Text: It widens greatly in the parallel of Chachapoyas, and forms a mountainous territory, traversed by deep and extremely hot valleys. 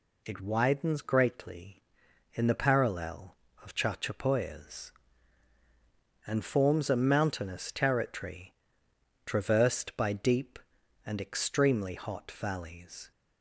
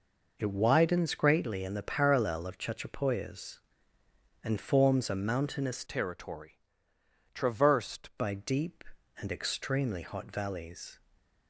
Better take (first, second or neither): first